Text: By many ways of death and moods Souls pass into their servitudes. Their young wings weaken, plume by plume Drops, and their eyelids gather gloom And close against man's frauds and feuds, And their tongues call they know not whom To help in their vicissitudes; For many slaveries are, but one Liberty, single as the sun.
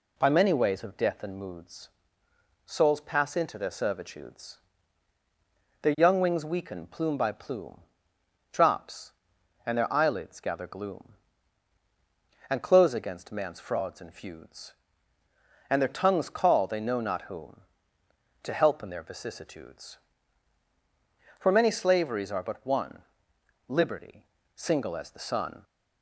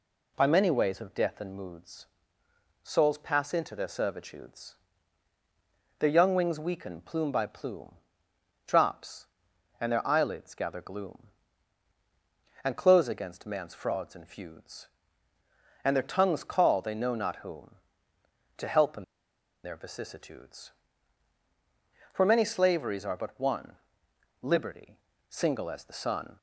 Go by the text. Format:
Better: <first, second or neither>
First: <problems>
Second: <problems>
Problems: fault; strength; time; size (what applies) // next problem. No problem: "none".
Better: first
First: pauses between "moods" and "Souls"; noticeable; at 1.8 s; 0.76 s long // pauses between "plume" and "Drops"; noticeable; at 7.7 s; 0.74 s long // pauses between "one" and "Liberty"; noticeable; at 23.0 s; 0.66 s long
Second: pauses between "moods" and "Souls"; noticeable; at 2.0 s; 0.76 s long // pauses between "plume" and "Drops"; noticeable; at 7.9 s; 0.74 s long // pauses between "in" and "their"; noticeable; at 19.0 s; 0.60 s long // pauses between "one" and "Liberty"; noticeable; at 23.7 s; 0.66 s long